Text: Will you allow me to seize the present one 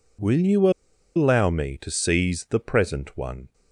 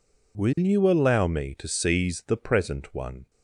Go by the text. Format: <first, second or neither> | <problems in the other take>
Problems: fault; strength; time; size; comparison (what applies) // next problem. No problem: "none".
second | pauses between "you" and "allow"; noticeable; at 0.6 s; 0.46 s long